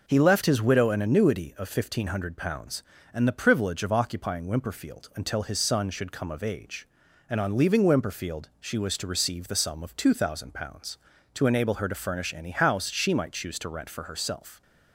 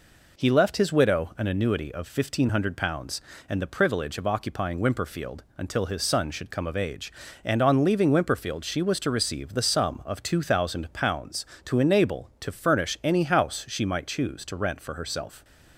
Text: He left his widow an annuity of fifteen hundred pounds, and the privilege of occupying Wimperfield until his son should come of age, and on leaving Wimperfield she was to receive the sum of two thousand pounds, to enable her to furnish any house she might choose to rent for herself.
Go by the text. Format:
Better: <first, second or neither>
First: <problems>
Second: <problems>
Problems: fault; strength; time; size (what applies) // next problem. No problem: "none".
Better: first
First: none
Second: skips "her"; at 12.3 s